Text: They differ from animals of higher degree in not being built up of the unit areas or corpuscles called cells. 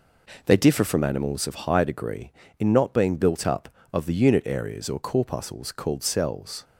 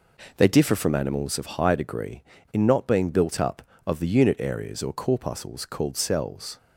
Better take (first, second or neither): neither